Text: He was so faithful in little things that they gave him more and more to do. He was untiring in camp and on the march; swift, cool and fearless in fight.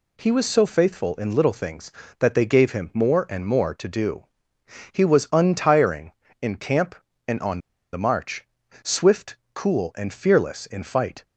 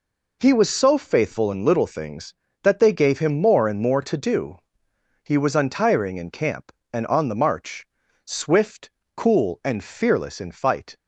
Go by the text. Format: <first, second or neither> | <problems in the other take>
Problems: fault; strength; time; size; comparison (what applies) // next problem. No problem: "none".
second | pauses between "on" and "the"; slight; at 7.5 s; 0.34 s long